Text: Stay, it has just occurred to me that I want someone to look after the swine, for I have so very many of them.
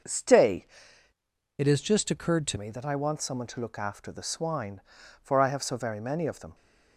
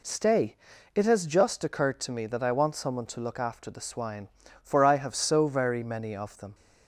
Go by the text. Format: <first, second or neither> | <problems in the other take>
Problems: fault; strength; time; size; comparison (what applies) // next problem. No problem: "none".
second | starts louder than the rest; until 2.0 s; 6 dB // changes voice from "it" to "to"; from 1.5 to 2.5 s; 1.0 s long